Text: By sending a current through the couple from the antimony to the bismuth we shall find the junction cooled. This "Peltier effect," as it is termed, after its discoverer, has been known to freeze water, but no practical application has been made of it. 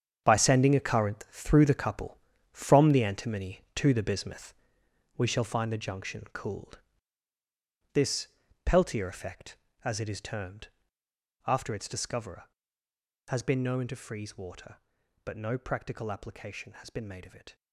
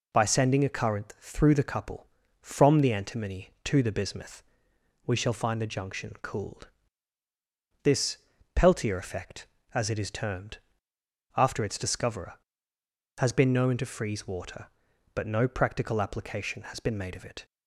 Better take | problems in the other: second | gets quieter; strong; throughout; 13 dB // pauses between "bismuth" and "we"; noticeable; at 4.5 s; 0.64 s long; noticeable in the second // pauses between "This" and "Peltier"; at 8.2 s; 0.38 s long; also in the second

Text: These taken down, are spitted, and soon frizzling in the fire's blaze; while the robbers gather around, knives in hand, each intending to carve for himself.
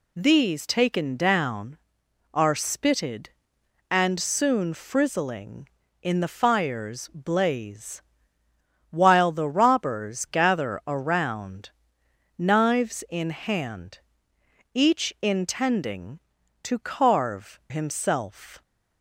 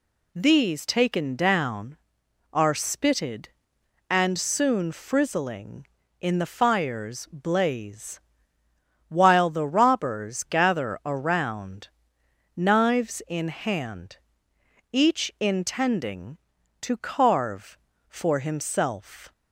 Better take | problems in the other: second | skips "for"; at 17.6 s

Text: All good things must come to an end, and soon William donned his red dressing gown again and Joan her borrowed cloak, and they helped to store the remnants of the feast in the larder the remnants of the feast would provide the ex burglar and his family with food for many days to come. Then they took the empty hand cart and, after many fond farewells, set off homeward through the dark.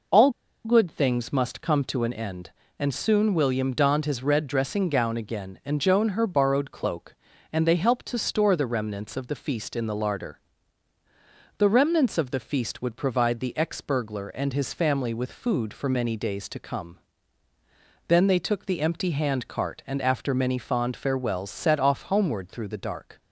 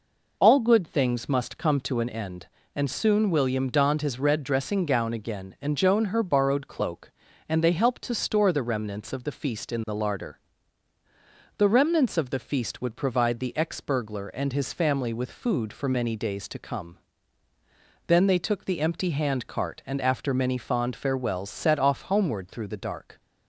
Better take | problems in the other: second | pauses between "All" and "good"; slight; at 0.2 s; 0.35 s long // pauses between "larder" and "the"; at 10.3 s; 1.1 s long; also in the second

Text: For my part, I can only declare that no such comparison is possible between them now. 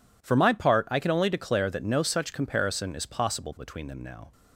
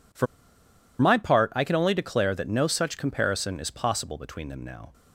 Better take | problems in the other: first | pauses between "For" and "my"; noticeable; at 0.2 s; 0.74 s long

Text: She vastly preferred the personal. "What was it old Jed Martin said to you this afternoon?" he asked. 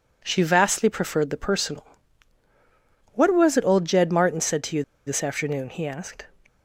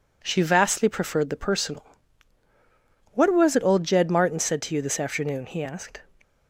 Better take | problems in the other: second | pauses between "you" and "this"; slight; at 4.8 s; 0.23 s long

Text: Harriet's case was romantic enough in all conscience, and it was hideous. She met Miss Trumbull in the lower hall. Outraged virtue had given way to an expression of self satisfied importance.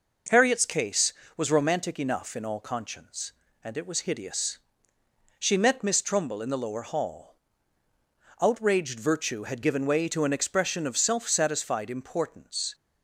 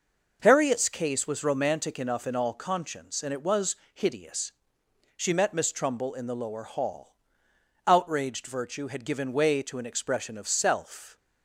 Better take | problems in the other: first | pauses between "was" and "hideous"; slight; at 3.7 s; 0.18 s long // stops before "satisfied importance"; at 11.1 s

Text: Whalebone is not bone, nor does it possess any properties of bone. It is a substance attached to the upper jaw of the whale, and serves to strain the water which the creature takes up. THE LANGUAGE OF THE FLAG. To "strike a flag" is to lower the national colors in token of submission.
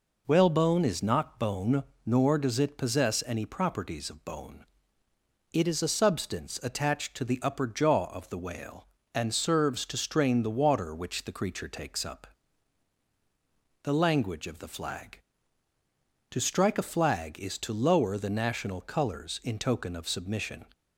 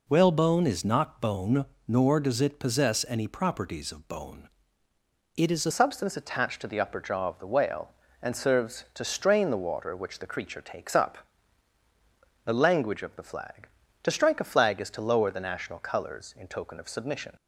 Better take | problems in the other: first | changes voice at "substance"; from 5.7 s on; 11.6 s long

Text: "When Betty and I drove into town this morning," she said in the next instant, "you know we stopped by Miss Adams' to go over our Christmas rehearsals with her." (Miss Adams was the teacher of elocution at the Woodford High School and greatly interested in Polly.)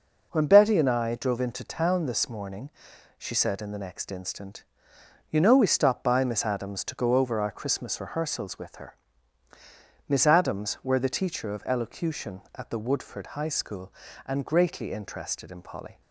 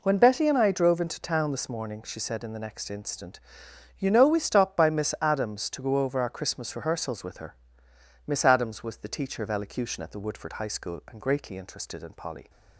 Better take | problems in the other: second | says "were" for "was"; at 10.8 s

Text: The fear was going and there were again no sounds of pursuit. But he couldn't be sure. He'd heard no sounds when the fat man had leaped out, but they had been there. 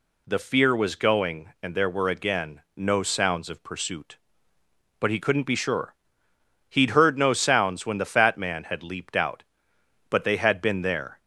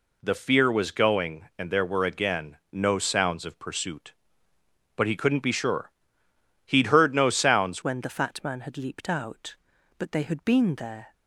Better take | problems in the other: first | pauses between "again" and "no"; slight; at 2.5 s; 0.16 s long; slight in the first // changes voice at "when"; from 7.8 s on; 3.3 s long

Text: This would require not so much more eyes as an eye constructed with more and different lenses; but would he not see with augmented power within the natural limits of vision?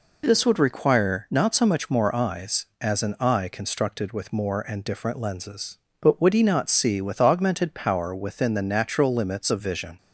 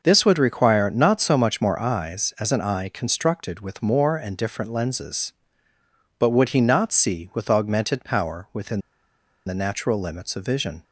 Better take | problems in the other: first | pauses between "within" and "the"; noticeable; at 8.7 s; 0.66 s long

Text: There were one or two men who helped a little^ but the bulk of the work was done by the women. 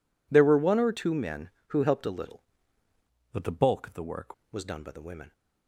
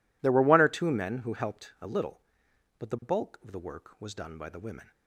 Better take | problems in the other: second | changes voice from "but" to "work"; from 3.3 to 4.3 s; 1.0 s long

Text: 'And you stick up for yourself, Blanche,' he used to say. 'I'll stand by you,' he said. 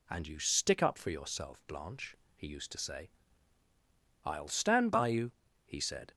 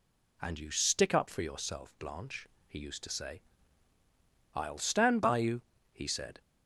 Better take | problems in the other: neither | none

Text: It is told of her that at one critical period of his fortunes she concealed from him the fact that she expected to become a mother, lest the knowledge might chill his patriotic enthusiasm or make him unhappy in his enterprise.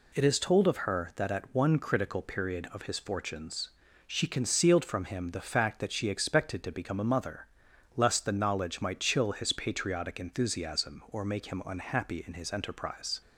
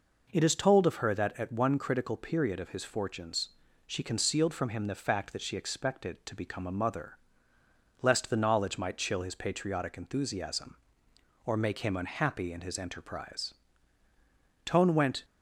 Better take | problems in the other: first | pauses between "fortunes" and "she"; at 3.4 s; 0.38 s long; slight in the first // goes on to say "Tone went"; from 14.6 s on; 0.60 s long

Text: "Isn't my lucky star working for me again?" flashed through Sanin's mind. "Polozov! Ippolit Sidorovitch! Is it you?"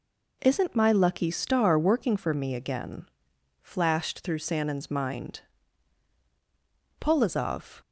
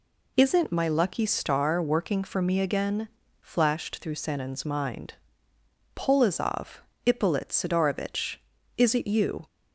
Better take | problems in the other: second | stops before "Ippolit Sidorovitch Is it you"; at 7.8 s

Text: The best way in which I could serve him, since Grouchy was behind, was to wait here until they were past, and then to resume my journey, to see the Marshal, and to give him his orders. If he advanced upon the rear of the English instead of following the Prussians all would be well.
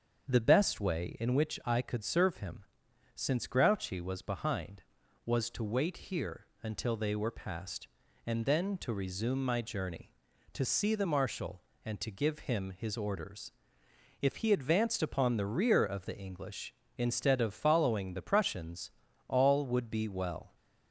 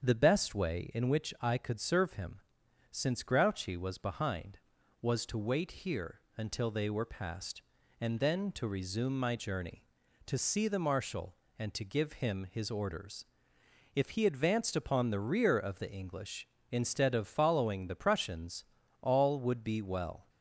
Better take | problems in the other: neither | starts louder than the rest; the same in both // pauses between "here" and "until"; slight; the same in both // pauses between "Prussians" and "all"; the same in both

